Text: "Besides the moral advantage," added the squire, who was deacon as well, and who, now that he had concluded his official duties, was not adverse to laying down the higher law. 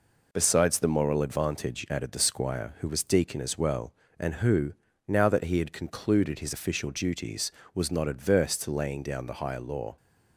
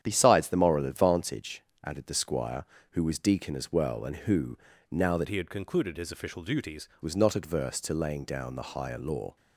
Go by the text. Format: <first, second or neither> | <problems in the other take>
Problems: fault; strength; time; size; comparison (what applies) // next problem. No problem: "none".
first | starts louder than the rest; strong; until 1.0 s; 9.5 dB // changes voice from "he" to "duties"; from 5.2 to 6.8 s; 1.6 s long